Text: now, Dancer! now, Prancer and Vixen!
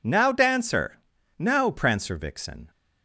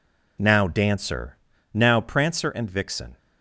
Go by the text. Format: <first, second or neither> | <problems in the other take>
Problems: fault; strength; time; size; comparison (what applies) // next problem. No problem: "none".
second | skips "and"; at 2.1 s